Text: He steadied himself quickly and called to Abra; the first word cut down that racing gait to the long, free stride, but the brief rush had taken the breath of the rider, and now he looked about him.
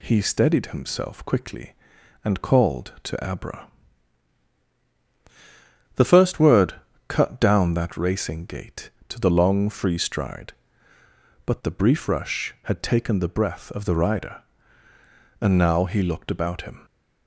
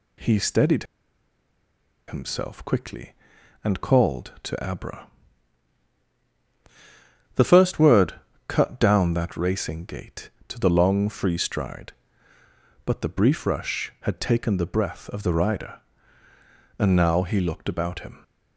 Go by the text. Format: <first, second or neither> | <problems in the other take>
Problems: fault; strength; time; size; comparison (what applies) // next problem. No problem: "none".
first | pauses between "steadied" and "himself"; at 0.8 s; 1.2 s long // pauses between "word" and "cut"; slight; at 8.1 s; 0.34 s long; slight in the first